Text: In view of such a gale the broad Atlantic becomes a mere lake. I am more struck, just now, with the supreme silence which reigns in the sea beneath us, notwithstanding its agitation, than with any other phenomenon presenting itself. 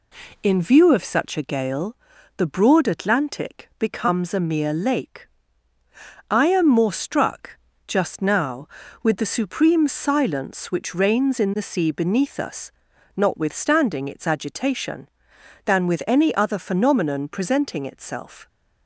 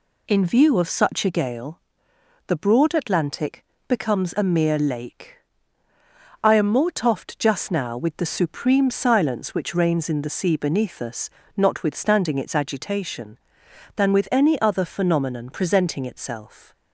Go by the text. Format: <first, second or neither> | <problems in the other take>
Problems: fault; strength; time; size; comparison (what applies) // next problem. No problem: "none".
first | pauses between "gale" and "the"; noticeable; at 1.8 s; 0.66 s long; also in the first // pauses between "Atlantic" and "becomes"; slight; at 3.6 s; 0.24 s long // says "toffed" for "struck"; at 6.9 s